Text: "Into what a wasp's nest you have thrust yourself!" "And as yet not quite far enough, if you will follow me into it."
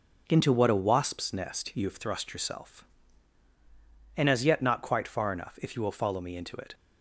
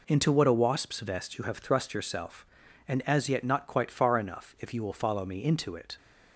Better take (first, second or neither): first